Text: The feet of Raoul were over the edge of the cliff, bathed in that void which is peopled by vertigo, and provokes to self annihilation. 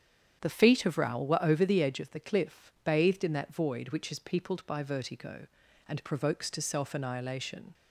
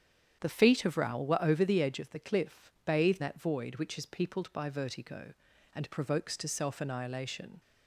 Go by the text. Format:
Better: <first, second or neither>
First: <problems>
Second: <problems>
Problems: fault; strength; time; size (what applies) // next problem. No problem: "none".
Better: first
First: starts louder than the rest; strong; until 1.4 s; 8.5 dB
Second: starts louder than the rest; strong; until 1.4 s; 9 dB // skips "in"; at 3.2 s